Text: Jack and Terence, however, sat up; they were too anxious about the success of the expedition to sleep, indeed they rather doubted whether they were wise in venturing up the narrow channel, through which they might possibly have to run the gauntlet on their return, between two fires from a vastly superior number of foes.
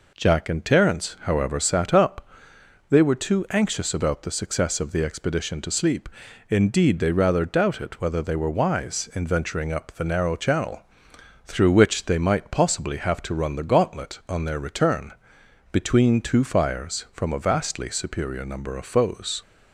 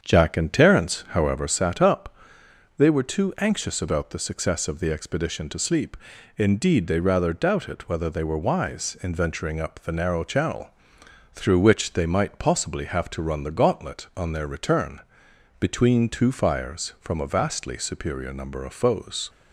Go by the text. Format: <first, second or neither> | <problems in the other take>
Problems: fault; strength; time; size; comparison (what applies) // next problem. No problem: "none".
first | starts louder than the rest; strong; until 1.4 s; 7.5 dB